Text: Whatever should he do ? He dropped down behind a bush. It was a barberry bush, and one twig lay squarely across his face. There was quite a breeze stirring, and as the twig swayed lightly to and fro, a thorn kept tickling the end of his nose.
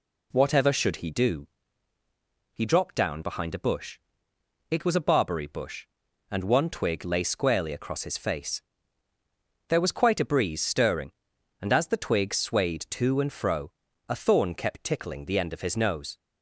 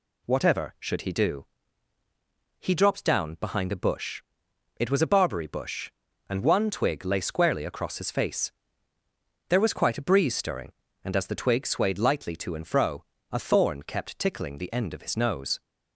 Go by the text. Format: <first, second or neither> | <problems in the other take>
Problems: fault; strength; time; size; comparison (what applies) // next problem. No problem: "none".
second | skips "lightly"; at 12.8 s